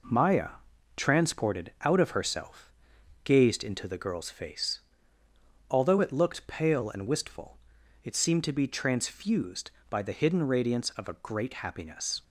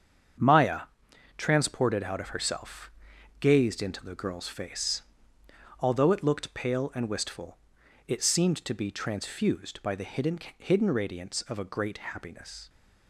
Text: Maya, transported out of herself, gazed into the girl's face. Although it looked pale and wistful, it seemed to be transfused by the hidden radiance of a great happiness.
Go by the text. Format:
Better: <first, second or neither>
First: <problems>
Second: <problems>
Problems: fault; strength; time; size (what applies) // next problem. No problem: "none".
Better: first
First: none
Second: starts louder than the rest; strong; until 1.9 s; 7.5 dB // says "hidden" twice; at 10.5 s